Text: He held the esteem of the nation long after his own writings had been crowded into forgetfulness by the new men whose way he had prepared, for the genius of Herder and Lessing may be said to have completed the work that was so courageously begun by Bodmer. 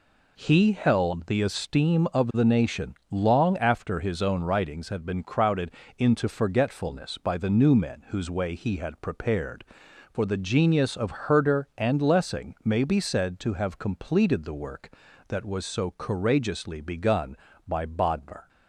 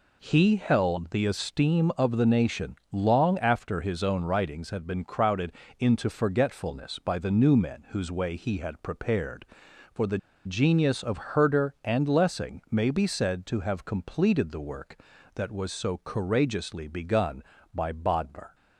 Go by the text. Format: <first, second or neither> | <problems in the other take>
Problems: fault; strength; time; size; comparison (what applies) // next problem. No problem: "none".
first | pauses between "nation" and "long"; slight; at 2.7 s; 0.16 s long; slight in the first // pauses between "crowded" and "into"; slight; at 5.5 s; 0.26 s long; slight in the first // pauses between "the" and "genius"; slight; at 10.1 s; 0.28 s long